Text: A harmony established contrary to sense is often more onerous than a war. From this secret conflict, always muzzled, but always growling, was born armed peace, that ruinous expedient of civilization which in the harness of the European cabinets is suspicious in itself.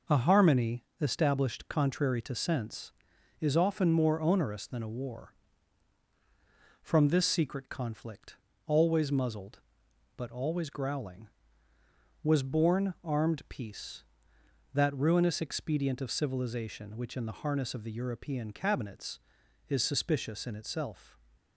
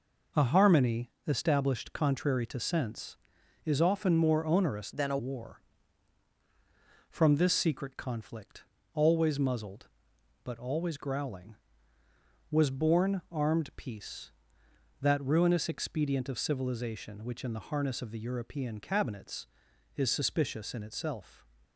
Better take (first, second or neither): first